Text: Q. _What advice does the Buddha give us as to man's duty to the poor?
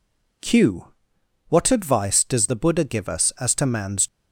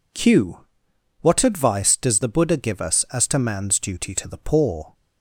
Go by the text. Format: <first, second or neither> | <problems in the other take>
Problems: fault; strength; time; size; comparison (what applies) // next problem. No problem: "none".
second | stops before "duty to the poor"; at 4.0 s